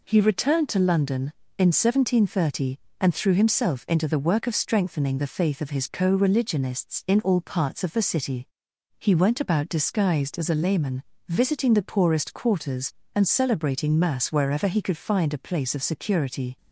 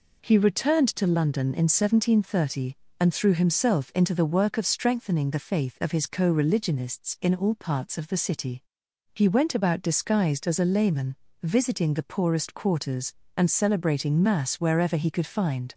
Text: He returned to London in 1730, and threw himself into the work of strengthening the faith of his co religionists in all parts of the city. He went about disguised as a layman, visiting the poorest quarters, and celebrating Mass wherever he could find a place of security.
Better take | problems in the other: first | stops before "a place of security"; at 15.7 s

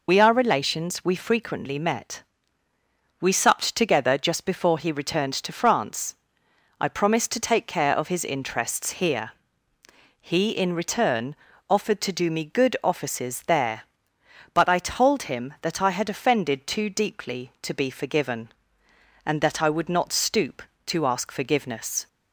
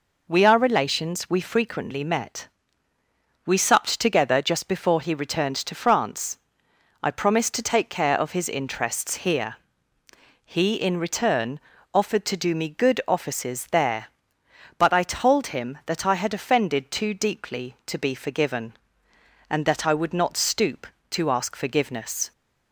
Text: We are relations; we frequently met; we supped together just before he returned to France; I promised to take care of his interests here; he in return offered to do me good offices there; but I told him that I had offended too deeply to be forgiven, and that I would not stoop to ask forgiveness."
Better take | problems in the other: second | loses the start of "We"; at 0.0 s; 45 ms // pauses between "return" and "offered"; slight; at 11.3 s; 0.34 s long; slight in the second

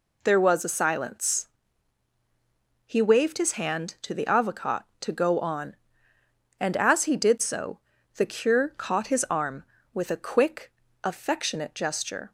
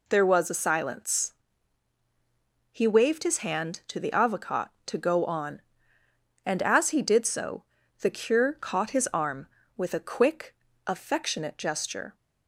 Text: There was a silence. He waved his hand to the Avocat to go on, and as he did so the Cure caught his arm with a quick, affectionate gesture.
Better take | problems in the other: neither | pauses between "so" and "the"; the same in both

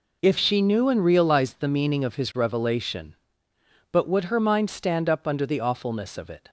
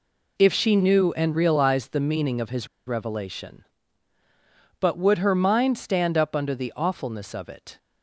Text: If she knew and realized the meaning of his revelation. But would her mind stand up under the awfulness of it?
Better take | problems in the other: first | pauses between "his" and "revelation"; slight; at 2.6 s; 0.20 s long

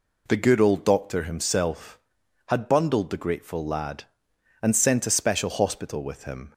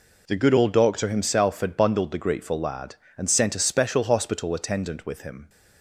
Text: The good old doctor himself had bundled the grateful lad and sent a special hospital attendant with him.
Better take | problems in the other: second | skips "attendant"; at 6.0 s

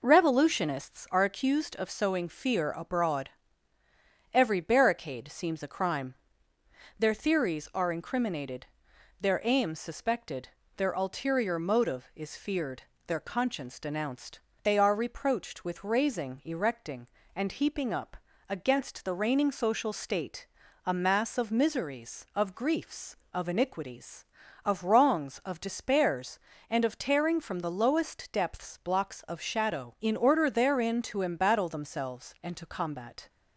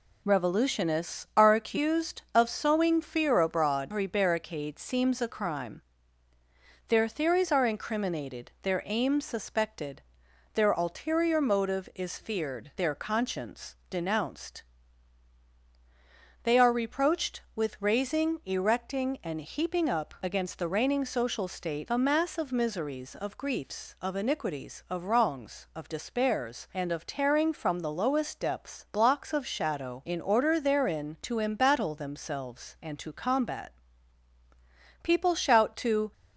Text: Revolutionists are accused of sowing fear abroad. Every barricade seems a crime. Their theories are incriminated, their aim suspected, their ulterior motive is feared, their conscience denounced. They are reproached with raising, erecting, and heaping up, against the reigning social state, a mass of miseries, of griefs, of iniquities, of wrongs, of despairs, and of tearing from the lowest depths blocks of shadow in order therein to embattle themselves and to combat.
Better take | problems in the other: first | goes on to say "People shout to"; noticeable; from 35.0 s on; 1.1 s long

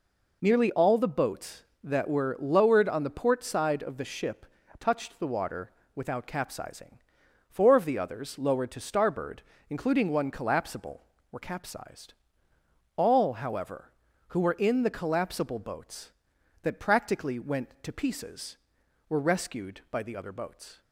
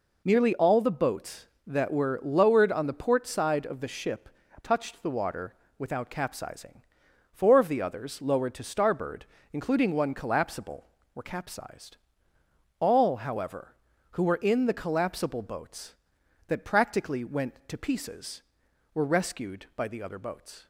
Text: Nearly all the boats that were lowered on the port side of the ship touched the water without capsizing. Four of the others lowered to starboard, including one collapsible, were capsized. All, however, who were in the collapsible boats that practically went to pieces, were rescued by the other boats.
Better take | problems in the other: neither | pauses between "ship" and "touched"; slight; the same in both // pauses between "water" and "without"; slight; the same in both

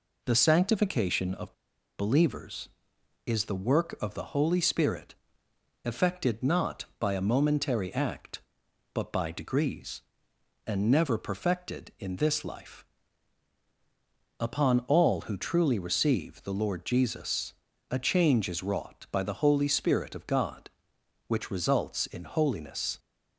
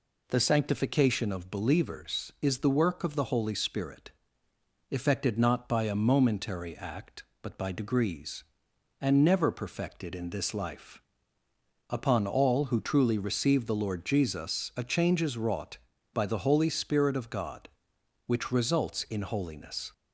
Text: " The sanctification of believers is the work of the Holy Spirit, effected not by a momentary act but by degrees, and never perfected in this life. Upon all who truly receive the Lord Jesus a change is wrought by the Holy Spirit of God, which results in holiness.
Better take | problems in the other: second | pauses between "of" and "believers"; at 1.5 s; 0.44 s long // pauses between "Jesus" and "a"; slight; at 17.5 s; 0.36 s long

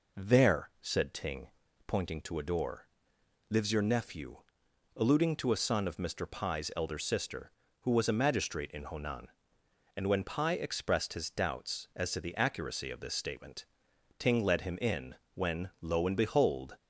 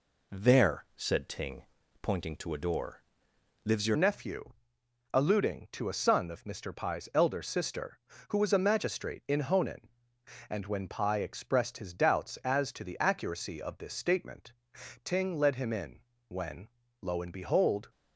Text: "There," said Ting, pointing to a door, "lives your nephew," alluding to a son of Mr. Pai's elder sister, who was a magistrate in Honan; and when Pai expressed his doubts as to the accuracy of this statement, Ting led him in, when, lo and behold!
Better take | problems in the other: first | changes voice at "nephew"; from 3.9 s on; 13.9 s long

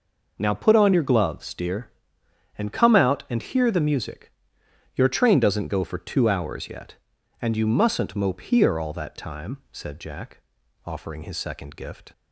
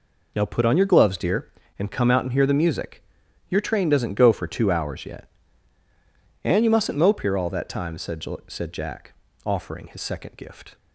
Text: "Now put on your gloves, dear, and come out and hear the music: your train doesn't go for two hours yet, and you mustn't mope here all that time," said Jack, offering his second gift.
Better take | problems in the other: first | says "said" twice; at 8.4 s

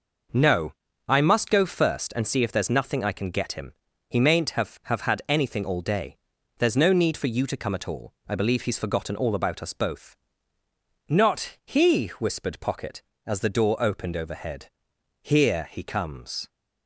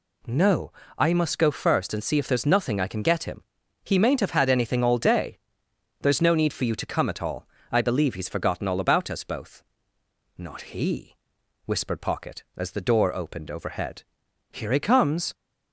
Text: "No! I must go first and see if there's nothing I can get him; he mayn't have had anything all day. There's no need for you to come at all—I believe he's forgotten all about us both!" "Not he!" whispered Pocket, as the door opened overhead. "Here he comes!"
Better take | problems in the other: second | says "have" twice; at 4.8 s

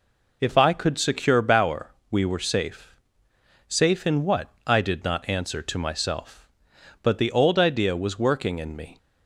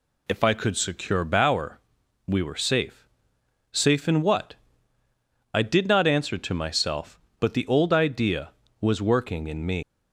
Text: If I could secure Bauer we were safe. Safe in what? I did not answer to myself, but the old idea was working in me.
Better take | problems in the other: first | pauses between "Bauer" and "we"; noticeable; at 1.7 s; 0.48 s long; slight in the first // leaves "me" unfinished; at 9.8 s; 165 ms

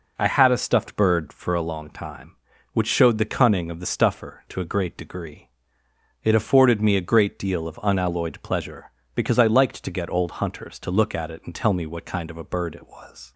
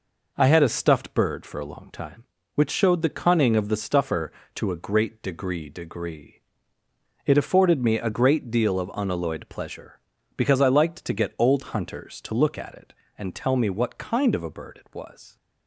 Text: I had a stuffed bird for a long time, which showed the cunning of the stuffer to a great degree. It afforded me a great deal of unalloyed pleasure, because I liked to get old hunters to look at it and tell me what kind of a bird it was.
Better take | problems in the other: first | says "degree" twice; at 5.6 s

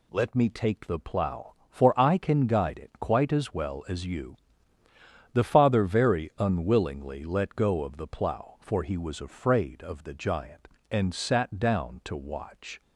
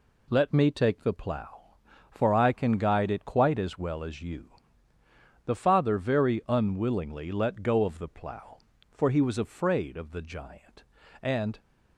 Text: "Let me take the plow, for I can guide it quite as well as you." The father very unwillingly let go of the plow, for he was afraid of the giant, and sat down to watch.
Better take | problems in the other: first | stops before "sat down to watch"; at 11.5 s

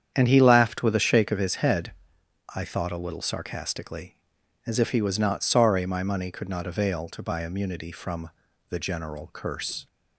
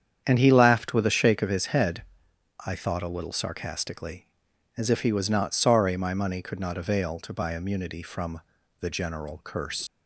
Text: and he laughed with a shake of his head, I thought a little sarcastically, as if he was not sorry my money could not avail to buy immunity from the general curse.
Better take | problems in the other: first | starts louder than the rest; strong; until 1.2 s; 8.5 dB; strong in the first // pauses between "from" and "the"; at 8.3 s; 0.40 s long; also in the first // leaves "curse" unfinished; at 9.8 s; 105 ms

